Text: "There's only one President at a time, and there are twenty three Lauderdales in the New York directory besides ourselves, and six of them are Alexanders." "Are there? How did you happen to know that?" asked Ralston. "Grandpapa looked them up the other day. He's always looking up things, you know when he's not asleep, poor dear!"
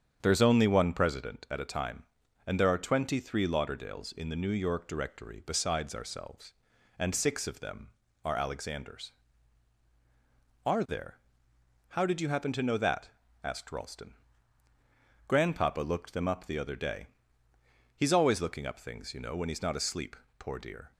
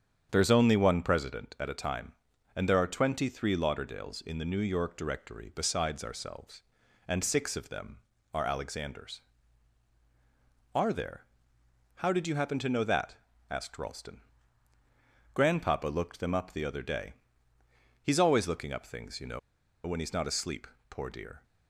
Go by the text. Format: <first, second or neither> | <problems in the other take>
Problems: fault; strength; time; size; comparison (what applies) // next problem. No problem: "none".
first | starts louder than the rest; strong; until 1.3 s; 8 dB; strong in the first // pauses between "know" and "when"; noticeable; at 19.3 s; 0.47 s long